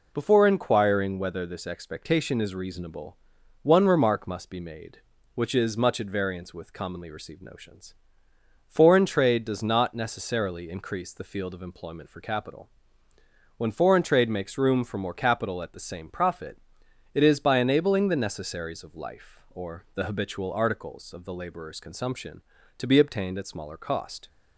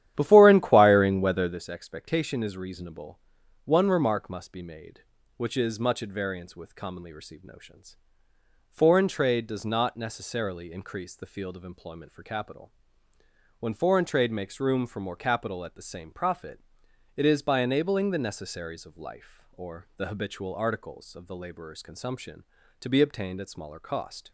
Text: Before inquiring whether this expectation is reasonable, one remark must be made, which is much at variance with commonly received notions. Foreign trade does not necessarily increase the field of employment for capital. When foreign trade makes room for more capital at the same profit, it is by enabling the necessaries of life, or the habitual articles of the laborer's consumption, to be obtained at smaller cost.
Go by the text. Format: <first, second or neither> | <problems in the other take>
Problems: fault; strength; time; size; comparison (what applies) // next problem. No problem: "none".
first | starts louder than the rest; strong; until 1.6 s; 11.5 dB